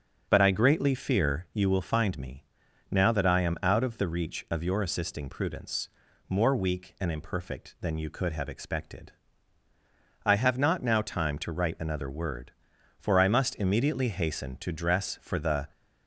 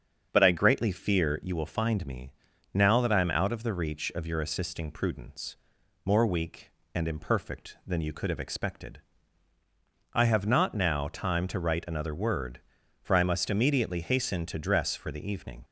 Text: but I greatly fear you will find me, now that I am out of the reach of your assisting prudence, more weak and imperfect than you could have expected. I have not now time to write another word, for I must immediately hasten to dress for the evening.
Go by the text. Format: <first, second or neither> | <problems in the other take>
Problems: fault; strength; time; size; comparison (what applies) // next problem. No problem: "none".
second | starts louder than the rest; until 1.2 s; 6.5 dB; also in the second // stops before "evening"; at 15.7 s